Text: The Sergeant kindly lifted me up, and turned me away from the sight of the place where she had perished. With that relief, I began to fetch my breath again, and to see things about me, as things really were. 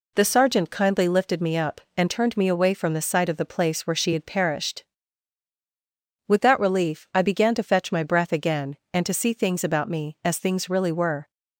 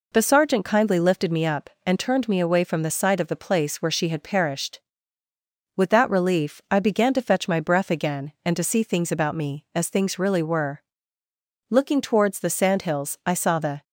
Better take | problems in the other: first | goes on to say "Looking towards the sandhills I saw the"; strong; from 11.6 s on; 2.1 s long

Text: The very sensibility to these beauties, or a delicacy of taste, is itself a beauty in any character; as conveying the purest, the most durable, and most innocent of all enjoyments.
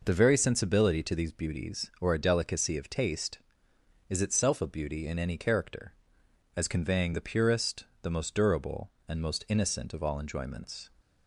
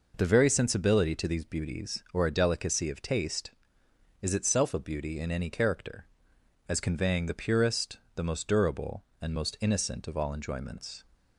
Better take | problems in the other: neither | none

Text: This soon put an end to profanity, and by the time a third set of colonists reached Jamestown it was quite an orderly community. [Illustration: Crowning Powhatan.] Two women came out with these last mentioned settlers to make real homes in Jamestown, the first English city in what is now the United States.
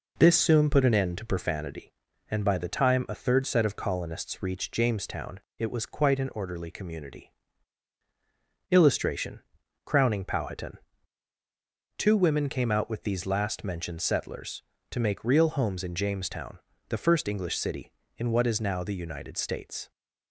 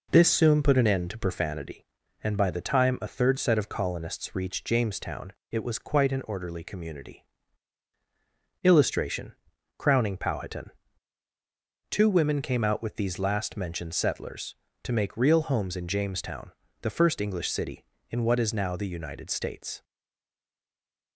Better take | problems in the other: first | pauses between "Jamestown" and "it"; slight; at 5.3 s; 0.18 s long; slight in the first // stays silent after the last word; noticeable; from 19.8 s on; 1.3 s long

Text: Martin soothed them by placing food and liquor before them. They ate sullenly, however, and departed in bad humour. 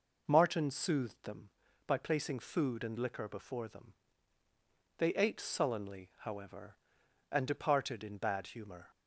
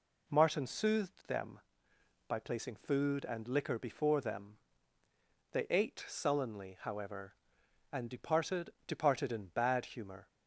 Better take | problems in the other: first | says "departed" twice; at 8.8 s

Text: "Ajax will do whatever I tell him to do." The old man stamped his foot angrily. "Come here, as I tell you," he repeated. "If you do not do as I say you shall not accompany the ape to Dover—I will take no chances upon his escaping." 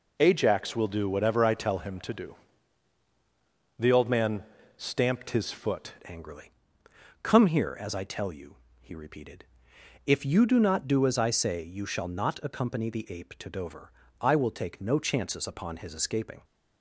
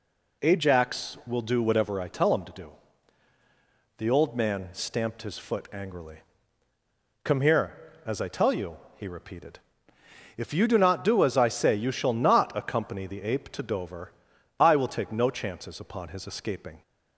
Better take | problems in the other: second | pauses between "man" and "stamped"; slight; at 4.4 s; 0.34 s long // changes voice at "angrily"; from 6.0 s on; 10.4 s long

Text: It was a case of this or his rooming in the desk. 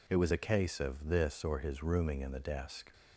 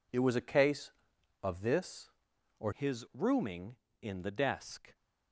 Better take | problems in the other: first | changes voice at "his"; from 2.7 s on; 2.2 s long

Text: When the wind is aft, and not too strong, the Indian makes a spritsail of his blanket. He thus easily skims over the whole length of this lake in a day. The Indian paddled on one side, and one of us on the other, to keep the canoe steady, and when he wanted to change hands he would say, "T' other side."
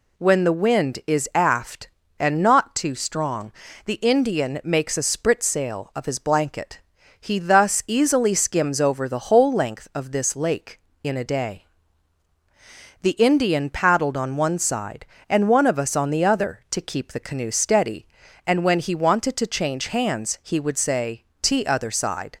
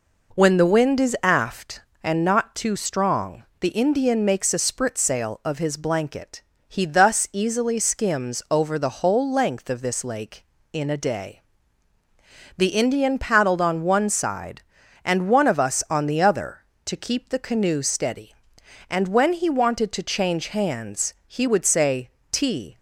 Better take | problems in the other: first | pauses between "hands" and "he"; slight; at 21.1 s; 0.16 s long // stops before "other side"; at 22.7 s

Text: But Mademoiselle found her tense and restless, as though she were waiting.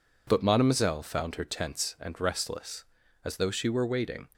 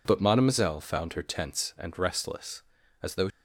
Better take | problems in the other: first | stops before "she were waiting"; at 3.3 s

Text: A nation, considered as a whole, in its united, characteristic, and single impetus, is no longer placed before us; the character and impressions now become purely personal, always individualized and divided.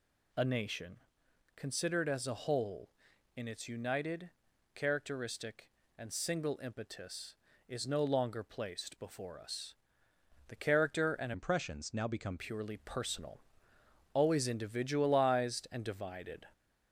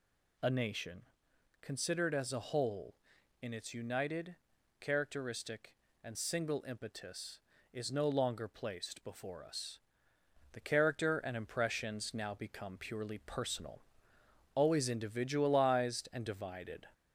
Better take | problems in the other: second | changes voice from "impressions" to "become"; from 11.3 to 12.3 s; 1.0 s long

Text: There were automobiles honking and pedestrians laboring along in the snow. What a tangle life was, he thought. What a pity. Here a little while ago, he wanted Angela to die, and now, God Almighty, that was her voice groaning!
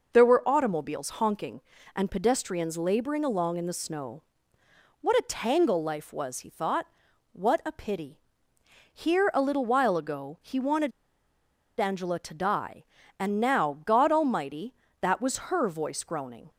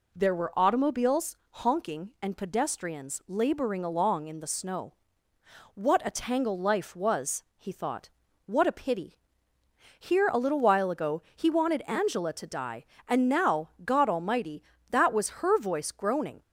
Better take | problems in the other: second | pauses between "wanted" and "Angela"; noticeable; at 10.9 s; 0.89 s long

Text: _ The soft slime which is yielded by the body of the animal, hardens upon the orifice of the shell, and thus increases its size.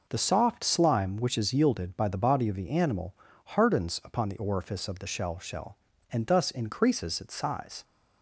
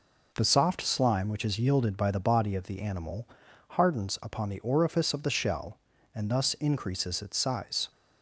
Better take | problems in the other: second | says "shell" twice; at 5.3 s

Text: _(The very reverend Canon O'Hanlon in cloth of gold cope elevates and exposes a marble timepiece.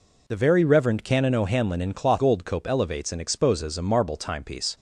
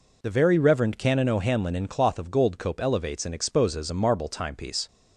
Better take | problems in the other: second | skips "of"; at 2.2 s

